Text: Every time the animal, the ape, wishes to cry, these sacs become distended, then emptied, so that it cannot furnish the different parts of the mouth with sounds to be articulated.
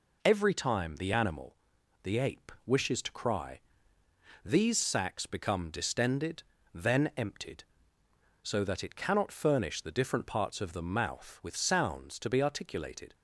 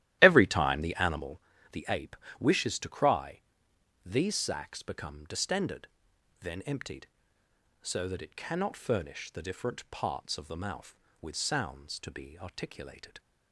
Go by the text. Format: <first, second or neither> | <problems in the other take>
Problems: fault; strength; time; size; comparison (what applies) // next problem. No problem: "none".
first | starts louder than the rest; strong; until 1.4 s; 14 dB